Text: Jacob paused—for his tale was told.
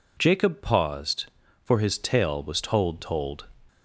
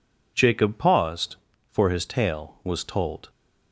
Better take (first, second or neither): second